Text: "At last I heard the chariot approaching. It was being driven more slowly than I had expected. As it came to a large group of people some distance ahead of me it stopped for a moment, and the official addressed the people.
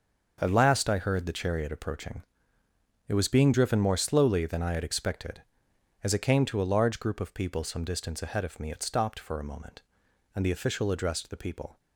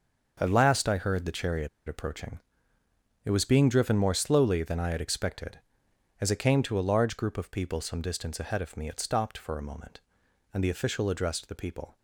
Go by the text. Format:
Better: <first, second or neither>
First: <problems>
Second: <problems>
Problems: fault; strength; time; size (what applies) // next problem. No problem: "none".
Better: first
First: starts louder than the rest; until 1.4 s; 6.5 dB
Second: starts louder than the rest; until 1.4 s; 6.5 dB // pauses between "chariot" and "approaching"; slight; at 1.6 s; 0.19 s long